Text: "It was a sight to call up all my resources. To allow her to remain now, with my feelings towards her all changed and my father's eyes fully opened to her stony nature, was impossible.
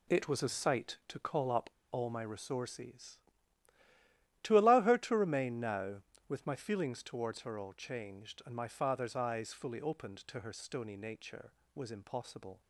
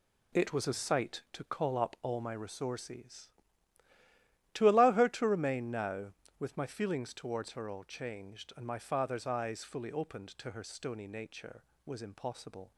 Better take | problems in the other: second | pauses between "up" and "all"; slight; at 1.6 s; 0.23 s long

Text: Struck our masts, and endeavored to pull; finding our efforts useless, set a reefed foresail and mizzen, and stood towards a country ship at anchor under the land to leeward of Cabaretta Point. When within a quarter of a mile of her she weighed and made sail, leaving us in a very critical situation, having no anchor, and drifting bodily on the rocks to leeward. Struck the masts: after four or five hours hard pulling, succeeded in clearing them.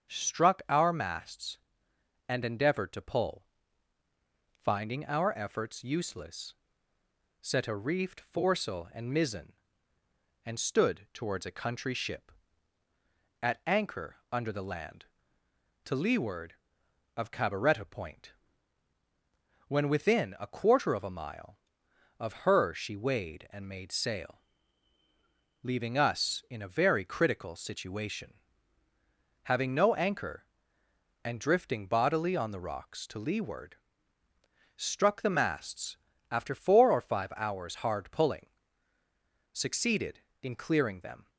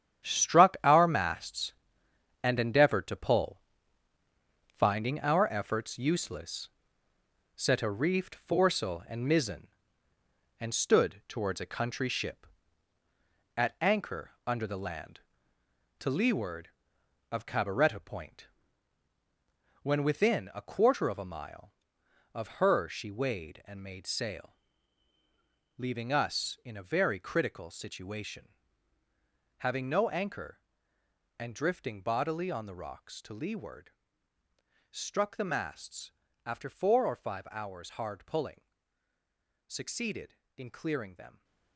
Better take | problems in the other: first | gets quieter; strong; throughout; 10 dB // starts louder than the rest; strong; until 1.3 s; 9.5 dB; strong in the first // pauses between "anchor" and "under"; slight; at 14.2 s; 0.16 s long; slight in the first

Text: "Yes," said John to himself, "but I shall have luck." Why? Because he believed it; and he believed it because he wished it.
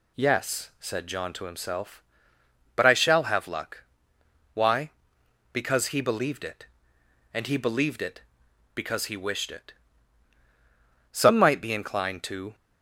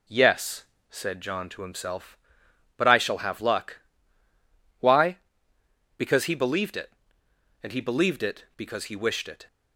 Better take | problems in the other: second | goes on to say "Some might be inclined to"; from 11.1 s on; 1.4 s long

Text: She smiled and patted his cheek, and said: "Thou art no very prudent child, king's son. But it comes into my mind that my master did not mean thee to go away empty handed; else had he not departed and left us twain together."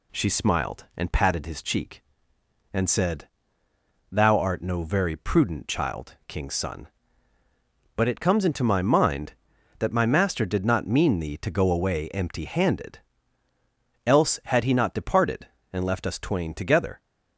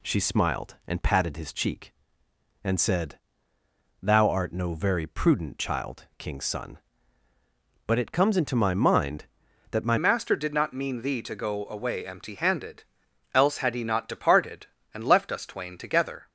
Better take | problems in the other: first | changes voice at "master"; from 9.9 s on; 6.3 s long

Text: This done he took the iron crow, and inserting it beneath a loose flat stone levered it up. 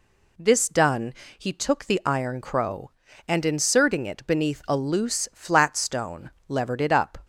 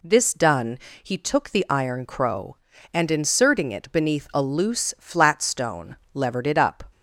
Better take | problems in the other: neither | pauses between "done" and "he"; slight; the same in both // pauses between "stone" and "levered"; slight; the same in both

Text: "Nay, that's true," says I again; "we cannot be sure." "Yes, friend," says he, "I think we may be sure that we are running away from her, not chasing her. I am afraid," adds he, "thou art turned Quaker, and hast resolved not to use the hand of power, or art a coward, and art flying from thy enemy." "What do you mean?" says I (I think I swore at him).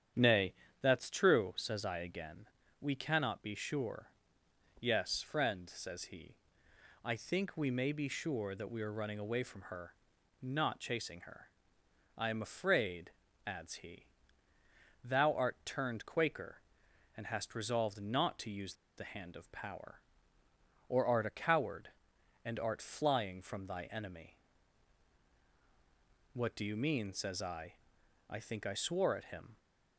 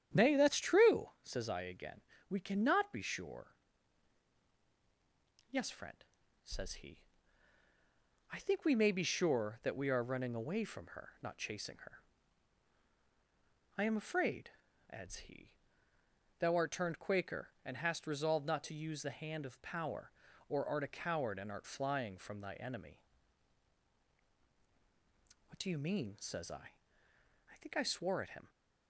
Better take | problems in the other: second | starts louder than the rest; strong; until 1.4 s; 9.5 dB; strong in the second // pauses between "use" and "the"; slight; at 18.7 s; 0.23 s long

